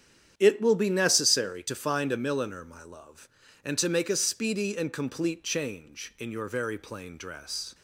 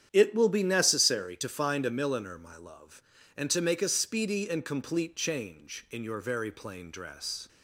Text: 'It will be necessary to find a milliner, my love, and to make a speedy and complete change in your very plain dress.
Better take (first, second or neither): neither